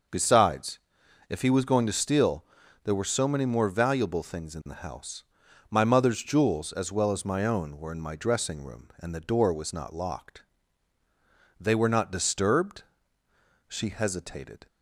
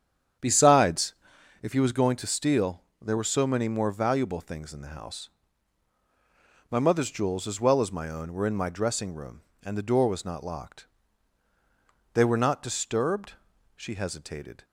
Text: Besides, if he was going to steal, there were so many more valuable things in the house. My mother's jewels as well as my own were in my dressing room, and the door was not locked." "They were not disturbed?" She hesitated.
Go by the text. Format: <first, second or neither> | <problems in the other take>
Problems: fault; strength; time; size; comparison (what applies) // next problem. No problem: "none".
first | starts louder than the rest; strong; until 1.4 s; 8.5 dB